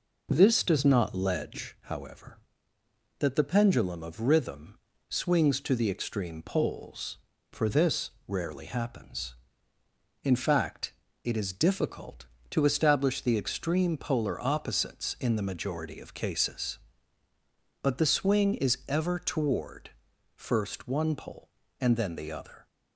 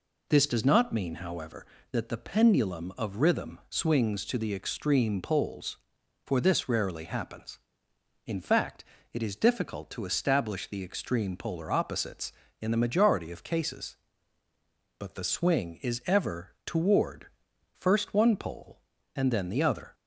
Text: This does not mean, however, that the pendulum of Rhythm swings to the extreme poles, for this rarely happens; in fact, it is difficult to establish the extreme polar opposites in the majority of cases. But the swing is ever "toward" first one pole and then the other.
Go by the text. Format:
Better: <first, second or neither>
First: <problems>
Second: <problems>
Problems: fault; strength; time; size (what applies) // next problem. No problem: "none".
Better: second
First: says "ledge" for "mean"; at 1.1 s // pauses between "Rhythm" and "swings"; slight; at 4.7 s; 0.30 s long // pauses between "this" and "rarely"; slight; at 8.1 s; 0.16 s long // pauses between "toward" and "first"; noticeable; at 19.8 s; 0.46 s long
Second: pauses between "toward" and "first"; noticeable; at 17.2 s; 0.48 s long